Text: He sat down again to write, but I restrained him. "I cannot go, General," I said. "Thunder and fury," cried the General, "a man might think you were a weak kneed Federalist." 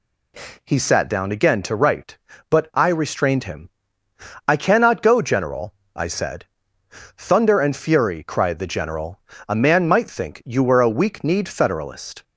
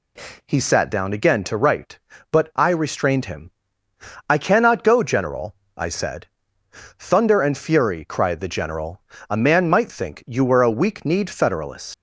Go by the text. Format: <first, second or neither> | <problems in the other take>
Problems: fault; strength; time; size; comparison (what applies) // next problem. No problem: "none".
first | leaves "Federalist" unfinished; at 11.9 s; 100 ms